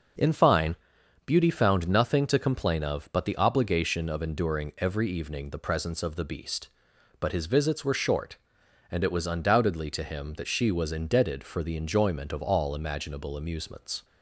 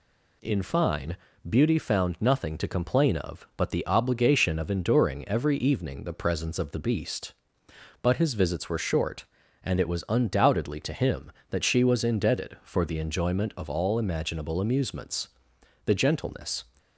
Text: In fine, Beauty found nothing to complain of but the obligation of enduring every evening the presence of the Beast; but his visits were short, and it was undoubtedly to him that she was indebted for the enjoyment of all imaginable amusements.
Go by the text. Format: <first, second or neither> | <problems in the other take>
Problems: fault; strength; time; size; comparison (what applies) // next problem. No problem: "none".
first | goes on to say "The gentleness"; noticeable; from 15.8 s on; 0.80 s long